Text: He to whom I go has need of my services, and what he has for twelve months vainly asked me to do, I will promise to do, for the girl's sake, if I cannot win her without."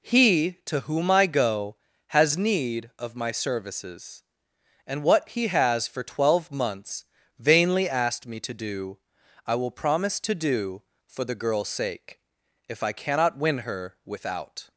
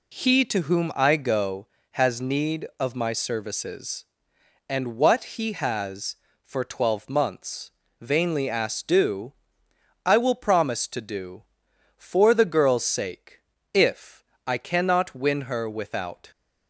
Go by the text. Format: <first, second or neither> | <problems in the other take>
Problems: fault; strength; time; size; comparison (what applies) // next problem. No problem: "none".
first | pauses between "months" and "vainly"; slight; at 7.7 s; 0.28 s long; slight in the first // skips "me to"; at 8.8 s // pauses between "if" and "I"; slight; at 14.2 s; 0.24 s long